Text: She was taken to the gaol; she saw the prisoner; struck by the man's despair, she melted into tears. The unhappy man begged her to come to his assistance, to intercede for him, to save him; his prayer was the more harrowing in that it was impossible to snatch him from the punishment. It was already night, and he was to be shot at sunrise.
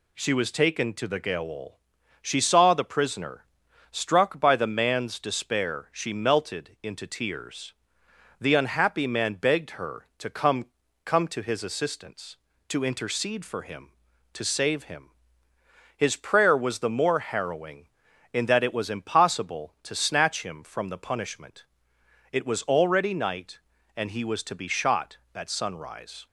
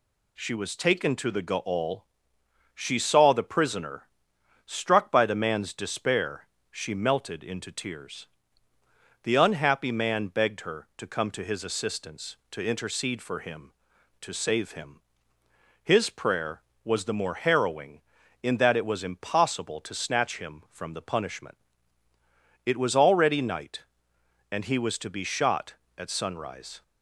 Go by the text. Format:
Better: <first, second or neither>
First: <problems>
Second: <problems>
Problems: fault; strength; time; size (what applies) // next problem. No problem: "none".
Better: second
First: says "come" twice; at 11.0 s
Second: none